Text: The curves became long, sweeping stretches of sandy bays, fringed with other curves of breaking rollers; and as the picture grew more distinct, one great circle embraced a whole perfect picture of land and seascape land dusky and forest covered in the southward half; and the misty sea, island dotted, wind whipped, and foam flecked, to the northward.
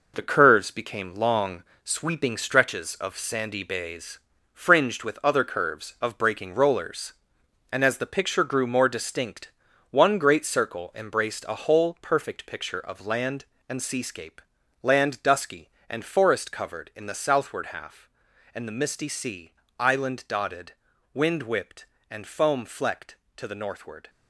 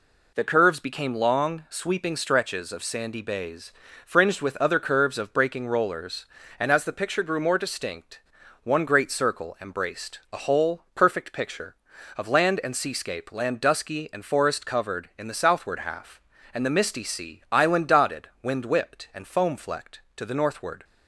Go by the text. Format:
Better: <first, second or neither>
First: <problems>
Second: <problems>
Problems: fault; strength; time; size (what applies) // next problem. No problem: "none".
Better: second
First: gets quieter; throughout; 7 dB // pauses between "seascape" and "land"; at 14.3 s; 0.44 s long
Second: none